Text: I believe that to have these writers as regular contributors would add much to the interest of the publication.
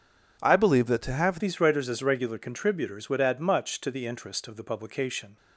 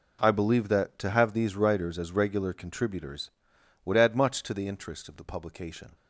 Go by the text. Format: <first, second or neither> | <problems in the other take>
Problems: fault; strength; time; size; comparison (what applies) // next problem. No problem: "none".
second | changes voice at "these"; from 1.3 s on; 4.0 s long